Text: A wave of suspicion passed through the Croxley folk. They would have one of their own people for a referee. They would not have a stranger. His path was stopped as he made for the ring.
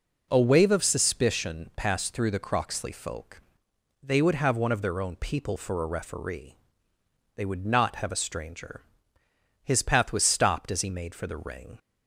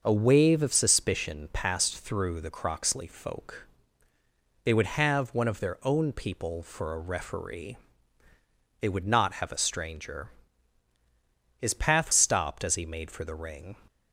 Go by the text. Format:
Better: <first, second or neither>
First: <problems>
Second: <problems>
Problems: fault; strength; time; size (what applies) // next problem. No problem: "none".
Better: first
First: none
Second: starts louder than the rest; until 1.0 s; 6 dB // skips "was"; at 12.1 s